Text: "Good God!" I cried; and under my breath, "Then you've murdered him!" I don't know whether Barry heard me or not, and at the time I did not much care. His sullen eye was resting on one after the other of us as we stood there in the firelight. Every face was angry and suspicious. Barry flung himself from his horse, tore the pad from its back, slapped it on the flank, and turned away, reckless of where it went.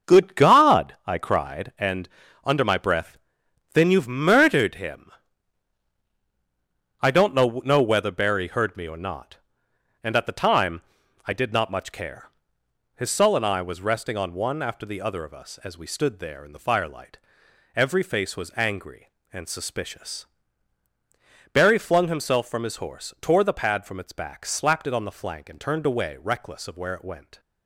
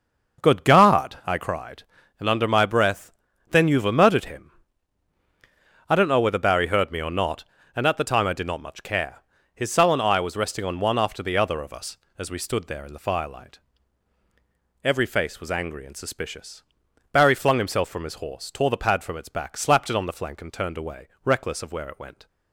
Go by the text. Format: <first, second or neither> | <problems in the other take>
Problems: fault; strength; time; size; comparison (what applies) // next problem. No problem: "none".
second | starts louder than the rest; until 1.1 s; 6.5 dB; noticeable in the second // pauses between "and" and "under"; slight; at 2.0 s; 0.36 s long // says "know" twice; at 7.6 s // pauses between "time" and "I"; at 10.8 s; 0.44 s long